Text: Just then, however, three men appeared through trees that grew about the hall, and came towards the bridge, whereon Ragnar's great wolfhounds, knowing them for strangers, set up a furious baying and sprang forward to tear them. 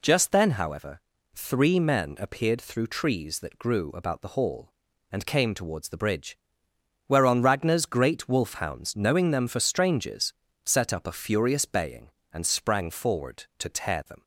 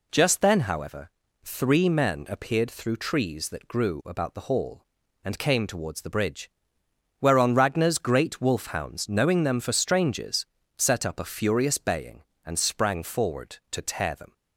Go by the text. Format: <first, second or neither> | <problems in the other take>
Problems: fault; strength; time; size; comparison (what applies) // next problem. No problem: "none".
neither | none